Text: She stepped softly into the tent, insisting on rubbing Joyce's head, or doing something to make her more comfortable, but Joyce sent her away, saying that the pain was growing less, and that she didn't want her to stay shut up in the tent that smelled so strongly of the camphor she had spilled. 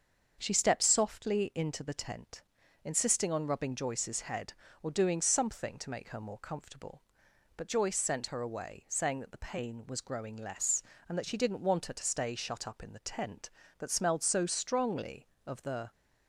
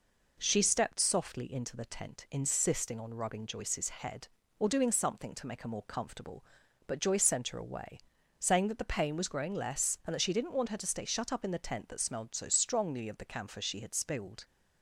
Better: second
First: starts louder than the rest; until 1.4 s; 6.5 dB // stops before "camphor she had spilled"; at 15.9 s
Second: none

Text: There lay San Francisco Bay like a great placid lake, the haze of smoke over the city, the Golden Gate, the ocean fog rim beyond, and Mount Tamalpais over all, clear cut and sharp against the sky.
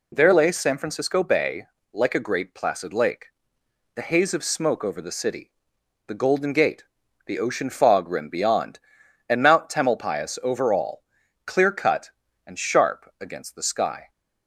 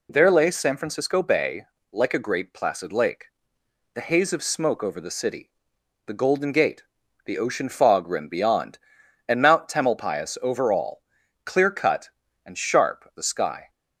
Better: first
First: pauses between "Bay" and "like"; slight; at 1.6 s; 0.26 s long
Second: pauses between "Bay" and "like"; slight; at 1.6 s; 0.26 s long // skips "against"; at 13.1 s

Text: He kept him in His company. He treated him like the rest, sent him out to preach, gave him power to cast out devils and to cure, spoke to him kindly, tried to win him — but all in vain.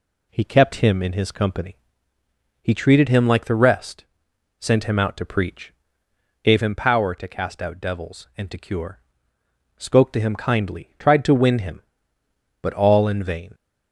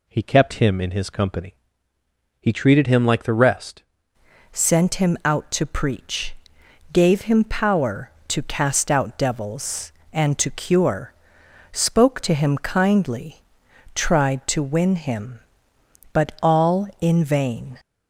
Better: first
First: none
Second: changes voice at "sent"; from 4.5 s on; 13.2 s long

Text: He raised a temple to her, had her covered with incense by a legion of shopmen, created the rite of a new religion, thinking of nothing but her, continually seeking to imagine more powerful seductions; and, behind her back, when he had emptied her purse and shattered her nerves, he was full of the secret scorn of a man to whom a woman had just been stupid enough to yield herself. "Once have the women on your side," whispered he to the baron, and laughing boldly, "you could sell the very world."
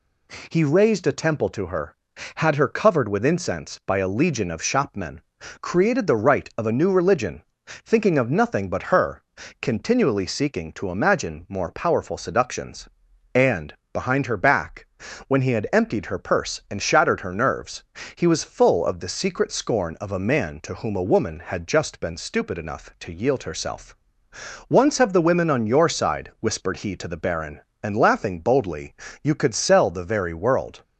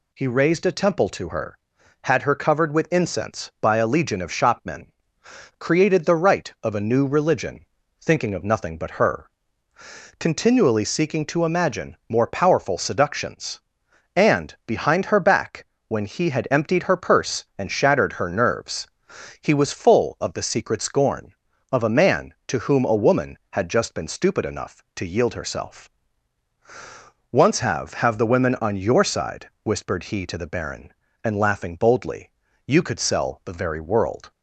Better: first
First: none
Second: says "have" twice; at 27.9 s

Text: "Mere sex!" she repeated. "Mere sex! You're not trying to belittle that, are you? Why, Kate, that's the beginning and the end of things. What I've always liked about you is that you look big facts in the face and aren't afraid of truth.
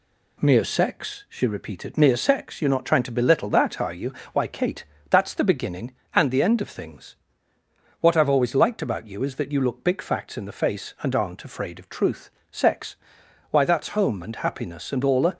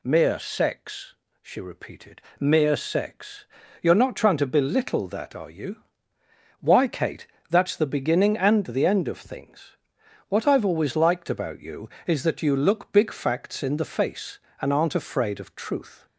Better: second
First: goes on to say "Sex Why that's home and happiness and all a"; strong; from 12.5 s on; 2.8 s long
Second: none

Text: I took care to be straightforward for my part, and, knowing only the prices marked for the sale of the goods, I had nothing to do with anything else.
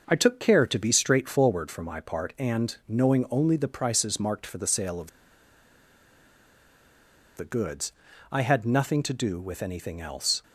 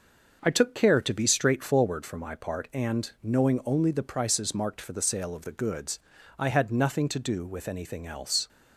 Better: second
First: starts louder than the rest; noticeable; until 1.0 s; 6 dB // pauses between "of" and "the"; strong; at 5.1 s; 2.2 s long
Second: starts louder than the rest; noticeable; until 1.4 s; 6 dB

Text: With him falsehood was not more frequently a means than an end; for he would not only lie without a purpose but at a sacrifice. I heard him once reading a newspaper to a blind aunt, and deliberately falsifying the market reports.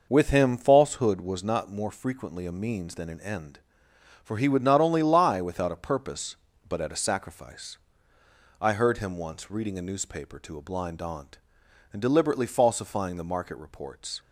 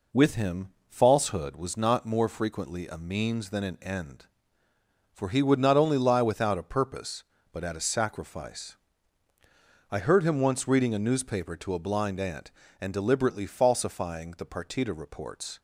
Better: first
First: none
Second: pauses between "him" and "falsehood"; slight; at 0.6 s; 0.20 s long // says "partita" for "market"; at 14.4 s

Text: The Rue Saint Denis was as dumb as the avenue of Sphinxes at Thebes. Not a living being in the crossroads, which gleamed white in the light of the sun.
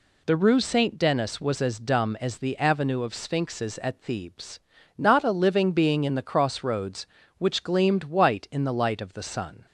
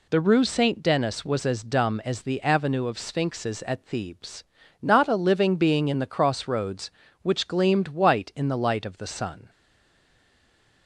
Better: first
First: none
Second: stays silent after the last word; noticeable; from 9.4 s on; 1.4 s long

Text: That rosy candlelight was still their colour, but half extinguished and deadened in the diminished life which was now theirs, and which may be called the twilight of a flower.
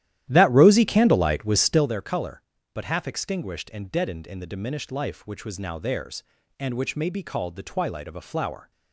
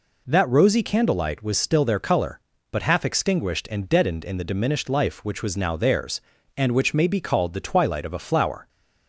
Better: second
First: starts louder than the rest; strong; until 1.9 s; 12.5 dB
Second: none

